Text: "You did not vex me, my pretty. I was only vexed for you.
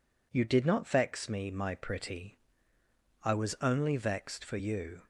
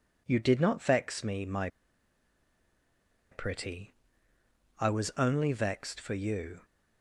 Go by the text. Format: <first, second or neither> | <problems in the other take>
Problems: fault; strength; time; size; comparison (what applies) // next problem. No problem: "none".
first | pauses between "my" and "pretty"; strong; at 1.6 s; 1.6 s long